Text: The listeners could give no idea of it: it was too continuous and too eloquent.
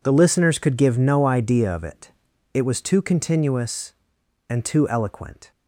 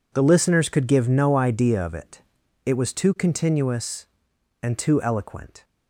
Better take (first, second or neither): neither